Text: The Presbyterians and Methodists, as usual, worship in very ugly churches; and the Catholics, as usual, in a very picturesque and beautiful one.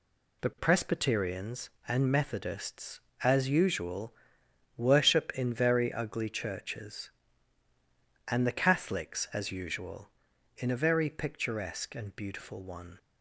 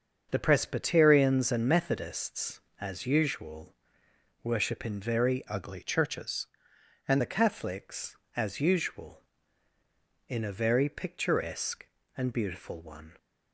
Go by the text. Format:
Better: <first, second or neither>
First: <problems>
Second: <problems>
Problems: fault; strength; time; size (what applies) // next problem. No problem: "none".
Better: first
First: none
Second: starts louder than the rest; until 1.3 s; 7 dB // changes voice from "ugly" to "and"; from 5.4 to 7.2 s; 1.8 s long